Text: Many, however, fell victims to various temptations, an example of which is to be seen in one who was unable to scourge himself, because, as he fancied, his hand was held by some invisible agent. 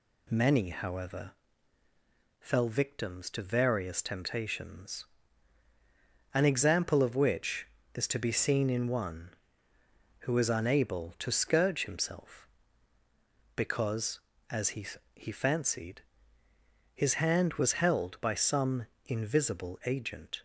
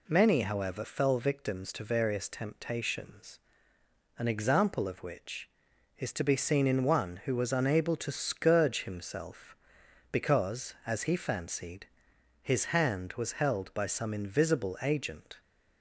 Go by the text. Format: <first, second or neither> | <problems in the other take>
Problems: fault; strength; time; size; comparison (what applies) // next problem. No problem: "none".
second | says "he" twice; at 15.1 s // pauses between "some" and "invisible"; slight; at 18.8 s; 0.20 s long